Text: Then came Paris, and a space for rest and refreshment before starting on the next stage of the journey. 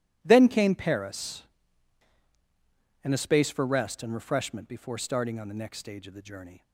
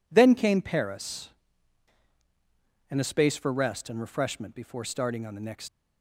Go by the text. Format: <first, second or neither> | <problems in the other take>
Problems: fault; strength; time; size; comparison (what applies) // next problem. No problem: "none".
first | stops before "stage of the journey"; at 5.6 s